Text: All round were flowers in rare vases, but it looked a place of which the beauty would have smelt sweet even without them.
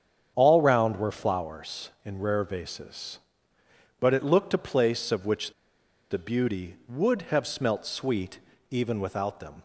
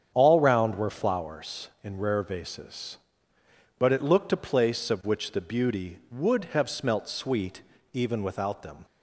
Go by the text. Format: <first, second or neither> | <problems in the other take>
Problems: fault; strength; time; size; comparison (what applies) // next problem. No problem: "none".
second | starts louder than the rest; strong; until 1.3 s; 8 dB; strong in the second // pauses between "which" and "the"; noticeable; at 5.5 s; 0.57 s long // pauses between "sweet" and "even"; slight; at 8.3 s; 0.32 s long; slight in the second